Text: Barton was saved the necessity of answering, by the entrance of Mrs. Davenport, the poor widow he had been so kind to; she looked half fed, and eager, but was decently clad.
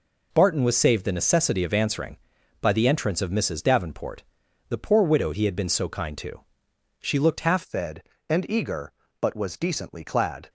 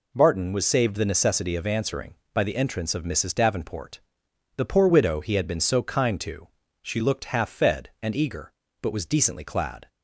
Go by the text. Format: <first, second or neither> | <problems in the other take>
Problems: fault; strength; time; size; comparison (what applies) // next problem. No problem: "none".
second | changes voice at "fed"; from 7.6 s on; 2.8 s long